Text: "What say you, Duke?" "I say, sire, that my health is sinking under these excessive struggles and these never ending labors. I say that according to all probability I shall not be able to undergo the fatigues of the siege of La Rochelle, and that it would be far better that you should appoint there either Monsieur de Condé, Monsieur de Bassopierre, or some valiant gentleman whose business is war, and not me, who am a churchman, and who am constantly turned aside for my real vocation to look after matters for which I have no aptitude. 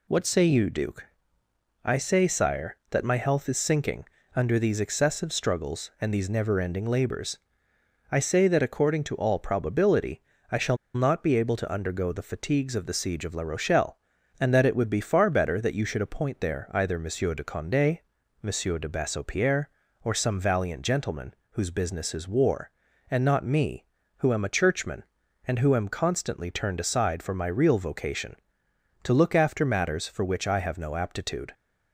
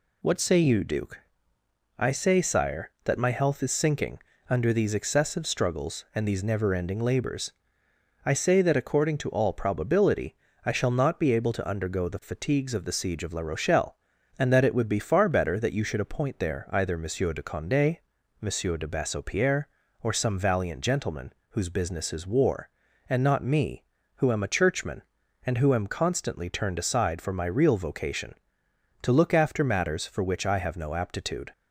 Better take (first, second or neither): second